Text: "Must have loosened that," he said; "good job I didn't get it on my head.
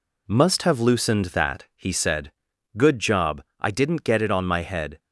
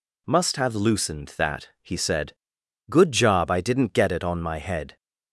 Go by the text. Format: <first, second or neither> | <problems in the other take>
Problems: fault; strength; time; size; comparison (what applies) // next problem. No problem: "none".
second | gets quieter; throughout; 6.5 dB // pauses between "job" and "I"; slight; at 3.4 s; 0.16 s long